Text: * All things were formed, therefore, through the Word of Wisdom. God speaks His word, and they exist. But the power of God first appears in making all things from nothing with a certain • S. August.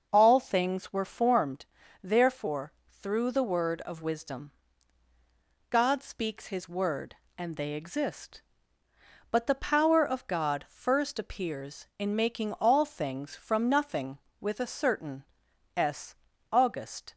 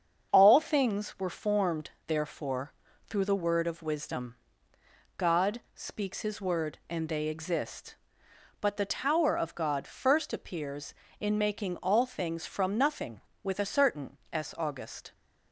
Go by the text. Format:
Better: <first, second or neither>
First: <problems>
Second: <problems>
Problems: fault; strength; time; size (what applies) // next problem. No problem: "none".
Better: first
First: starts louder than the rest; noticeable; until 1.1 s; 6 dB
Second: starts louder than the rest; strong; until 1.3 s; 7 dB // says "tower" for "power"; at 8.8 s